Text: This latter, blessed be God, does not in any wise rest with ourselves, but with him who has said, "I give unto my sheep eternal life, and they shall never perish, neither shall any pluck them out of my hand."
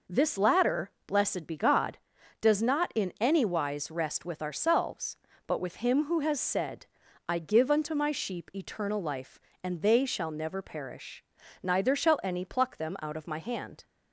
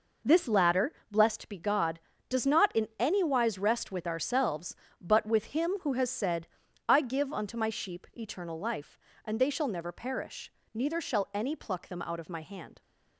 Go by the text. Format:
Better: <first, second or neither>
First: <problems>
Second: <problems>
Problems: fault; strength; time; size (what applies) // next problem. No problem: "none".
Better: neither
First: none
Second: none